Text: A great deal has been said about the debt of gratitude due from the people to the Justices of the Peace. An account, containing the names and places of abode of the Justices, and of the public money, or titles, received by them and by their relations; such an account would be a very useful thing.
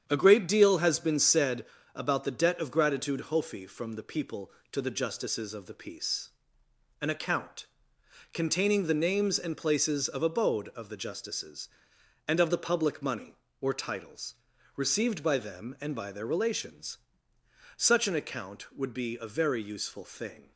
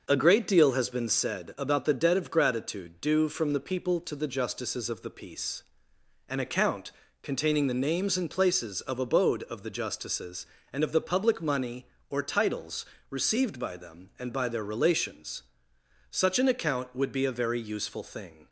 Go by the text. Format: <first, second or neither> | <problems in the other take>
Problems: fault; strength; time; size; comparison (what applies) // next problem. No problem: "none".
second | starts louder than the rest; strong; until 1.0 s; 8.5 dB; noticeable in the second // pauses between "said" and "about"; slight; at 1.6 s; 0.30 s long // says "hofi" for "due"; at 3.2 s